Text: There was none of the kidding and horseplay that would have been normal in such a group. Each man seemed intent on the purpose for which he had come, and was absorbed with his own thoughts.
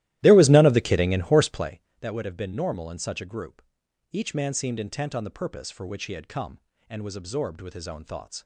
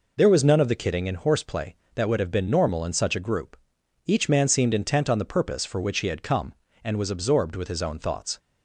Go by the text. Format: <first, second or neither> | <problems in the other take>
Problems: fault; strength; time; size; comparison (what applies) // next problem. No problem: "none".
second | starts louder than the rest; strong; until 1.8 s; 15 dB